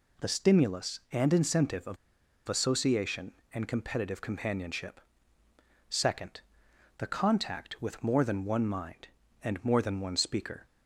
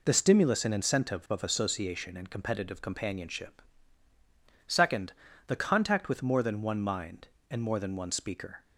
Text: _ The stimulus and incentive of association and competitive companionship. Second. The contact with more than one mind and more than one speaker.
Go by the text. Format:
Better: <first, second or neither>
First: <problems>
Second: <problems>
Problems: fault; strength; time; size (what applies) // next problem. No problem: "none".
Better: second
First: pauses between "of" and "association"; noticeable; at 1.9 s; 0.51 s long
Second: none